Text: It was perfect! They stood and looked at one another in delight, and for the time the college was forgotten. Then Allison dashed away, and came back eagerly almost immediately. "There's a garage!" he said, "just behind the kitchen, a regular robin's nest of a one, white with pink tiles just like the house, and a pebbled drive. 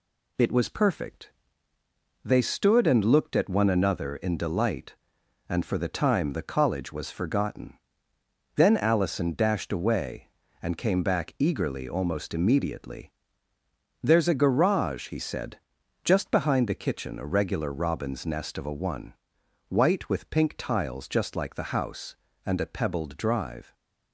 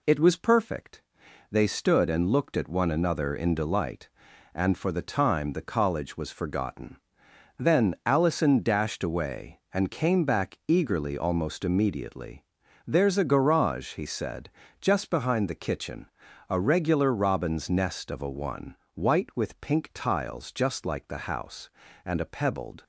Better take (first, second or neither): first